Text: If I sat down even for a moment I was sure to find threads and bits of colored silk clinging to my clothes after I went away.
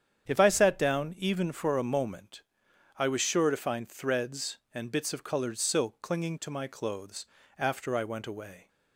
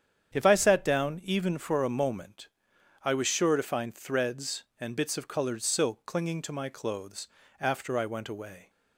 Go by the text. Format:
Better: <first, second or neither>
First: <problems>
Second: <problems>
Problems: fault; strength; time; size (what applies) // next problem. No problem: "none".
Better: neither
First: starts louder than the rest; strong; until 1.3 s; 8.5 dB // pauses between "moment" and "I"; noticeable; at 2.4 s; 0.56 s long // pauses between "clothes" and "after"; slight; at 7.2 s; 0.32 s long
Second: starts louder than the rest; strong; until 1.3 s; 8.5 dB // pauses between "moment" and "I"; noticeable; at 2.4 s; 0.56 s long // pauses between "clothes" and "after"; slight; at 7.2 s; 0.32 s long